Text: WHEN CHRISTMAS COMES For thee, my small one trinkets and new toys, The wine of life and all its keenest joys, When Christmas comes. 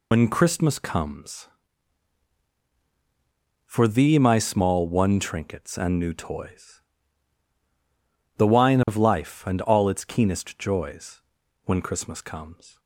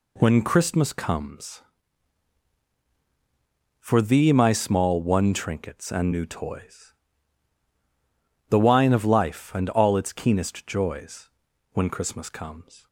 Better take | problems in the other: second | loses the start of "WHEN"; at 0.1 s; 95 ms

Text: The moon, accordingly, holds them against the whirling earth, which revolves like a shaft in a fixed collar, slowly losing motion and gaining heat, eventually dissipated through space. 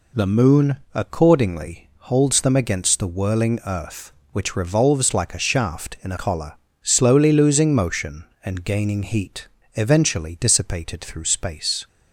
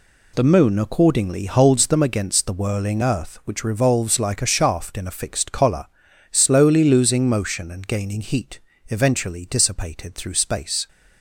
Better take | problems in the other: second | skips "fixed"; at 6.1 s

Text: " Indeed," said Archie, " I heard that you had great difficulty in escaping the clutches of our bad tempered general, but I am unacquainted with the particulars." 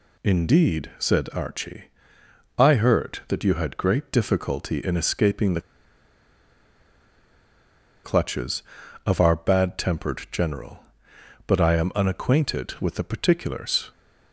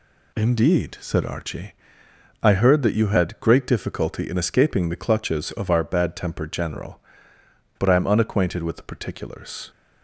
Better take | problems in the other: second | pauses between "the" and "clutches"; strong; at 5.5 s; 2.4 s long

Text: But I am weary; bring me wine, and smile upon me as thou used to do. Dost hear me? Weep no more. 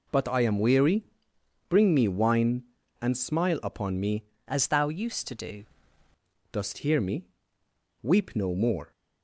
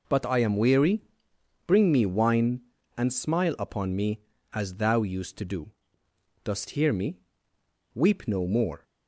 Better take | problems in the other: second | changes voice from "as" to "do"; from 4.4 to 5.6 s; 1.2 s long

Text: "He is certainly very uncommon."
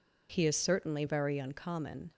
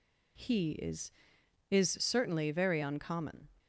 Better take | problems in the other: first | says "is" twice; at 1.7 s

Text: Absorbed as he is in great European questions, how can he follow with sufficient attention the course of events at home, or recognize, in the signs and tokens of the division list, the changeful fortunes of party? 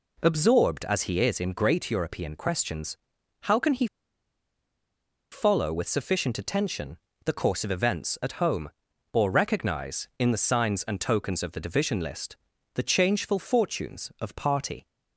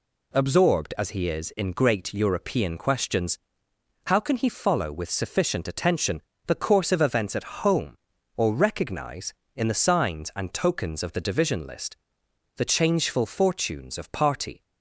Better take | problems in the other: second | pauses between "he" and "follow"; strong; at 3.8 s; 1.4 s long // pauses between "attention" and "the"; slight; at 6.9 s; 0.26 s long; slight in the second

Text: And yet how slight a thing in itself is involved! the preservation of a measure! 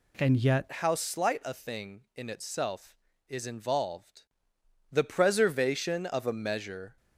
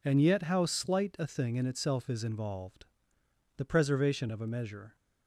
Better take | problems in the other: second | changes voice at "how"; from 0.7 s on; 6.2 s long

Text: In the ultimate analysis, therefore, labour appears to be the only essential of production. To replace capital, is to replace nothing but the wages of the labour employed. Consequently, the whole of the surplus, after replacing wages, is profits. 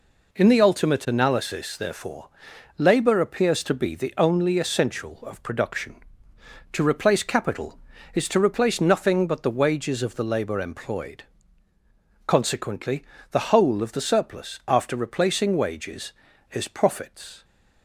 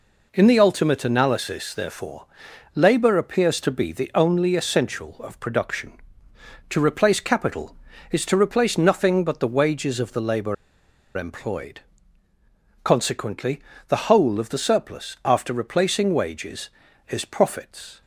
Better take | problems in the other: first | pauses between "labour" and "employed"; noticeable; at 10.5 s; 0.61 s long

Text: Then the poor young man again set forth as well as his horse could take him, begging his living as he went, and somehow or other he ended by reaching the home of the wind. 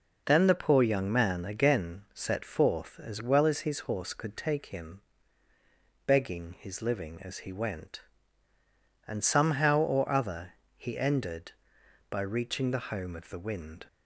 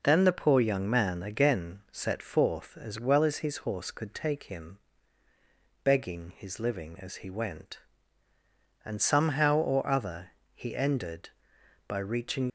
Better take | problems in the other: first | pauses between "other" and "he"; slight; at 10.3 s; 0.24 s long; slight in the first // stops before "the home of the wind"; at 12.4 s

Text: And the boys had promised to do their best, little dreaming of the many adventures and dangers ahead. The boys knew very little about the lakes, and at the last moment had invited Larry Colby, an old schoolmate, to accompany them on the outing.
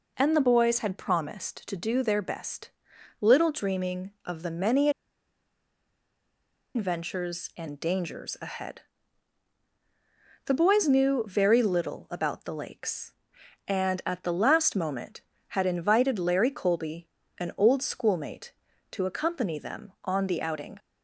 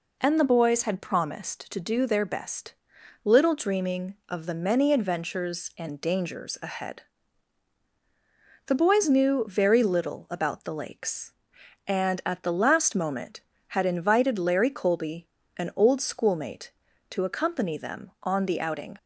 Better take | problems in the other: second | pauses between "many" and "adventures"; strong; at 4.8 s; 1.8 s long

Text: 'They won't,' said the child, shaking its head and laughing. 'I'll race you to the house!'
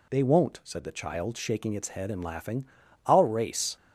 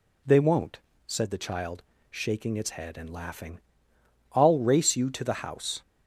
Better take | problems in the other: second | stops before "you to the house"; at 3.7 s

